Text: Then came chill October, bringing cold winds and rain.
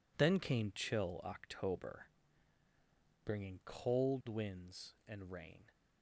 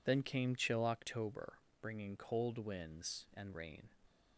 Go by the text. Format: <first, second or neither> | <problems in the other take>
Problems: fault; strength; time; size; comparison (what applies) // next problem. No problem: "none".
neither | none